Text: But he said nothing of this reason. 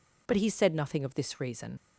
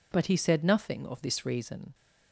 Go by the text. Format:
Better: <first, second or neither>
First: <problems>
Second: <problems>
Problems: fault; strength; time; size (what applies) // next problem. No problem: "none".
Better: second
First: leaves "reason" unfinished; at 1.7 s; 80 ms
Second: none